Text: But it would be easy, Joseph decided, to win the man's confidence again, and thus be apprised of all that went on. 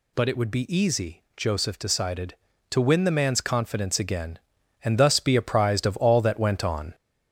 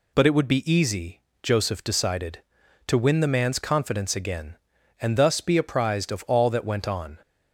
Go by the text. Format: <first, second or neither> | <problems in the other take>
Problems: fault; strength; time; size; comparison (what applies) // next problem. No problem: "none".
second | gets louder; noticeable; throughout; 4 dB